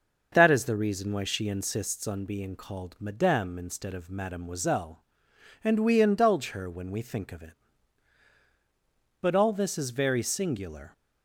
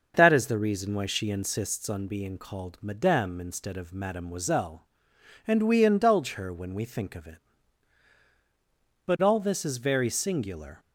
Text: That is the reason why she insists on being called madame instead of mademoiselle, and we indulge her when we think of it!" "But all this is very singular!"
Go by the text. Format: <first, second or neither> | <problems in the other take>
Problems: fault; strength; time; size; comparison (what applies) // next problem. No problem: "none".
neither | starts louder than the rest; the same in both